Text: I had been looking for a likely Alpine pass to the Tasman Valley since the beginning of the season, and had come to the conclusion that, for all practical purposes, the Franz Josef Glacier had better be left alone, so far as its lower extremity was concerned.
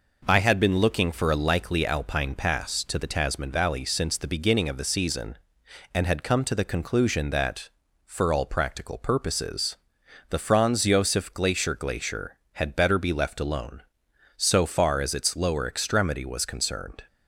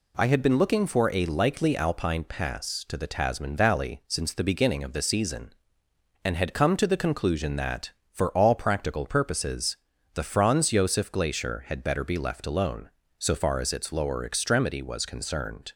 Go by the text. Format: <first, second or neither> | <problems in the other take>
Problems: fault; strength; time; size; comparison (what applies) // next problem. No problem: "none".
second | says "Glacier" twice; at 11.7 s